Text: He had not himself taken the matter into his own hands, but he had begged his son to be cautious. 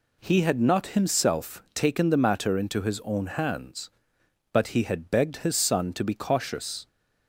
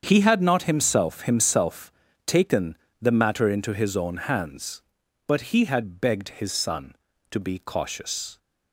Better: first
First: none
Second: starts louder than the rest; strong; until 1.0 s; 7.5 dB // says "himself" twice; at 1.2 s // pauses between "taken" and "the"; slight; at 2.7 s; 0.24 s long

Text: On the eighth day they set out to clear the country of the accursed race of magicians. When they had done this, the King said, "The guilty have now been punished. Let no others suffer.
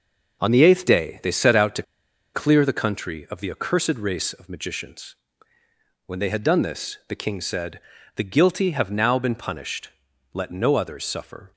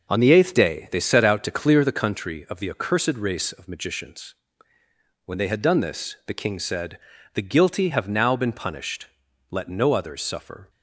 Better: second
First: pauses between "to" and "clear"; noticeable; at 1.8 s; 0.51 s long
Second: none

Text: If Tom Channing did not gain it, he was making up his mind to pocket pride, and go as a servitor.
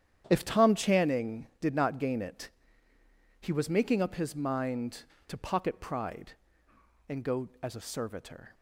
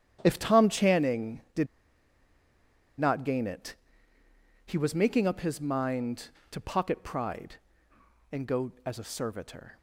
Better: first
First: starts louder than the rest; strong; until 1.2 s; 9.5 dB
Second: starts louder than the rest; strong; until 1.2 s; 9.5 dB // pauses between "did" and "not"; strong; at 1.6 s; 1.3 s long

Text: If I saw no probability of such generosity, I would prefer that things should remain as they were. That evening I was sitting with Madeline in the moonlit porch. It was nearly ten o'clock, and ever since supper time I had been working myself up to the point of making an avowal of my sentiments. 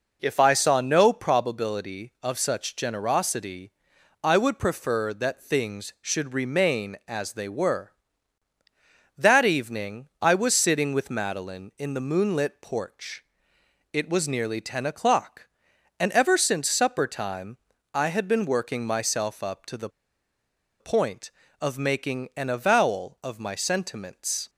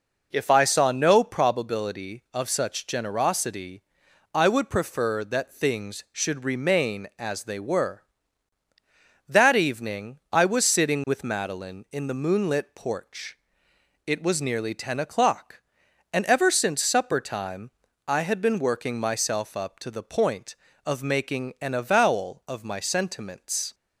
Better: second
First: pauses between "time" and "I"; at 17.5 s; 0.38 s long // pauses between "the" and "point"; noticeable; at 19.8 s; 0.91 s long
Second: pauses between "time" and "I"; at 17.6 s; 0.38 s long

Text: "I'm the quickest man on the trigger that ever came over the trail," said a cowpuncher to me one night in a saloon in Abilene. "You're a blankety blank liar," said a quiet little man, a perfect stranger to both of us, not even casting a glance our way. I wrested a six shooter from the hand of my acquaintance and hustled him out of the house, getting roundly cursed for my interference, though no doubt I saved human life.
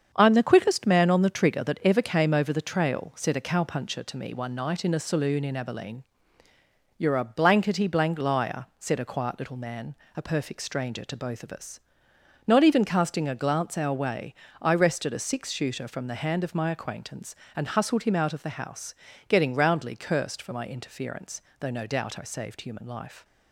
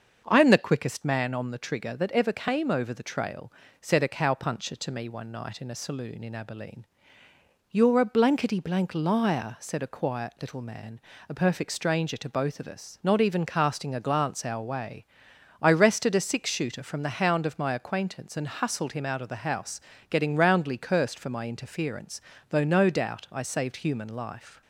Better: first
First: starts louder than the rest; strong; until 1.1 s; 7.5 dB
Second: starts louder than the rest; until 1.2 s; 6.5 dB // says "hound" for "hand"; at 17.1 s

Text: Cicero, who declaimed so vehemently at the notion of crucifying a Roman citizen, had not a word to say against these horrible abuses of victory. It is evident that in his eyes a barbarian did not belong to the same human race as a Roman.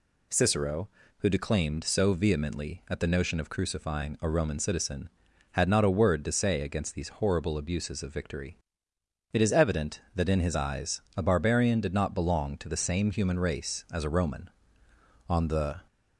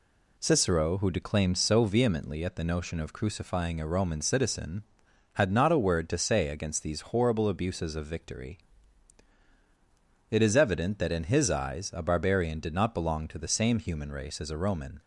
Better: second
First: goes on to say "On the"; from 15.2 s on; 0.58 s long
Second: none

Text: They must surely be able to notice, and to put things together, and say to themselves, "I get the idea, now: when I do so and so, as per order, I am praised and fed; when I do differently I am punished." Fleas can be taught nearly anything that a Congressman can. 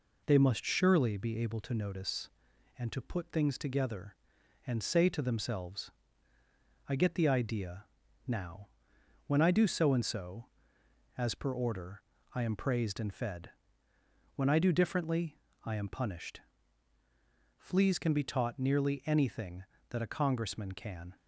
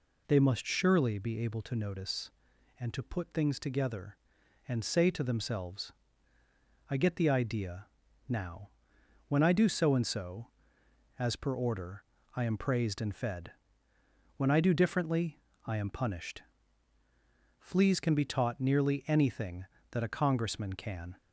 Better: second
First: gets quieter; slight; throughout; 2 dB // pauses between "differently" and "I"; slight; at 15.3 s; 0.26 s long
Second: pauses between "differently" and "I"; slight; at 15.4 s; 0.26 s long

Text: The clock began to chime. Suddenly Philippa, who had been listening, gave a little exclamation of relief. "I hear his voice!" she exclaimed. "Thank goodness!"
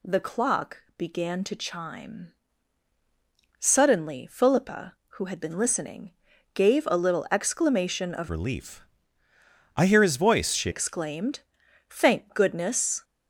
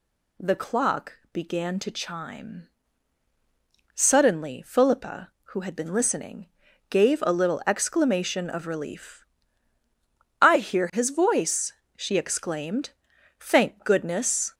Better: second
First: changes voice from "relief" to "she"; from 8.2 to 10.6 s; 2.4 s long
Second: none

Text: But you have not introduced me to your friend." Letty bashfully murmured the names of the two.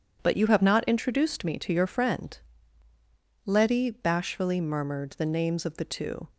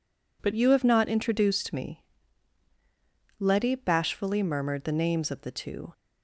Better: first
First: none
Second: skips "to your friend"; at 2.7 s

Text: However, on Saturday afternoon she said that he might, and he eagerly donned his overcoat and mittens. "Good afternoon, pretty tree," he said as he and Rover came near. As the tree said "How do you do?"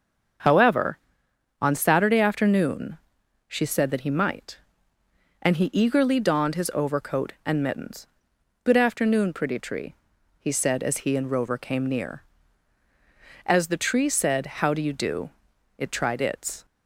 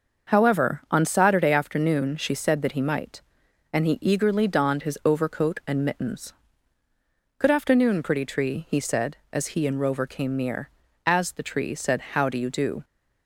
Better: second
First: starts louder than the rest; until 2.0 s; 6.5 dB // pauses between "afternoon" and "she"; noticeable; at 2.9 s; 0.50 s long // goes on to say "it tried its"; noticeable; from 15.7 s on; 0.88 s long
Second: starts louder than the rest; until 1.3 s; 6 dB

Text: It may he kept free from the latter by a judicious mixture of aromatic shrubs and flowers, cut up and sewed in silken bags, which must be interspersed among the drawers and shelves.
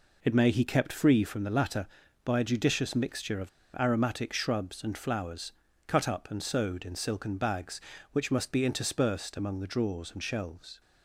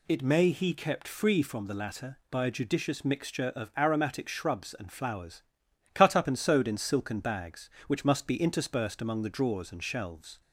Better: second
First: pauses between "of" and "aromatic"; slight; at 3.4 s; 0.30 s long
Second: none

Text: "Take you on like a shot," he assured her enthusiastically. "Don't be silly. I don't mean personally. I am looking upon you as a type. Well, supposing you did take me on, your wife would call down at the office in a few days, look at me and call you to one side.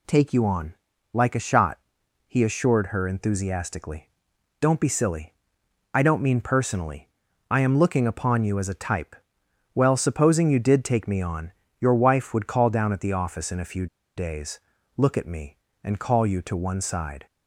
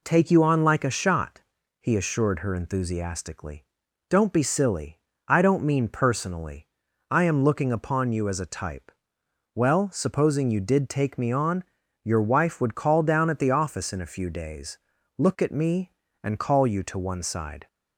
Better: second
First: pauses between "on" and "like"; at 0.7 s; 0.38 s long // pauses between "few" and "days"; slight; at 13.8 s; 0.31 s long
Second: none

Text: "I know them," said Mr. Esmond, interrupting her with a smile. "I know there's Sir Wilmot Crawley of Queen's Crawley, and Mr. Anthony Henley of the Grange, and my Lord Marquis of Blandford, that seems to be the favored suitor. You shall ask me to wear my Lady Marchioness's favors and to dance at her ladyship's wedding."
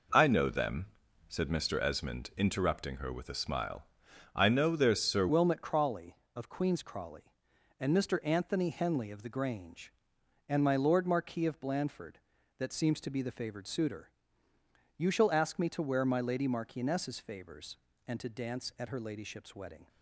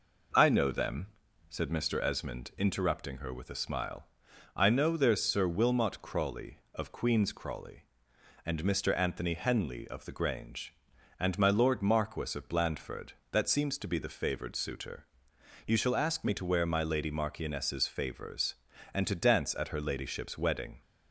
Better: second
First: changes voice at "Wilmot"; from 5.2 s on; 14.6 s long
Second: none

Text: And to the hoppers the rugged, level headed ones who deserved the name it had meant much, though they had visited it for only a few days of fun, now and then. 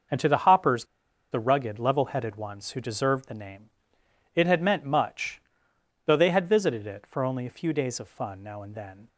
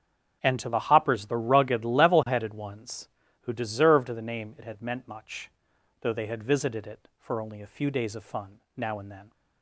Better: second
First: starts louder than the rest; noticeable; until 1.5 s; 6 dB // pauses between "hoppers" and "the"; noticeable; at 0.8 s; 0.47 s long // pauses between "name" and "it"; noticeable; at 3.6 s; 0.64 s long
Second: starts louder than the rest; strong; until 1.4 s; 7 dB

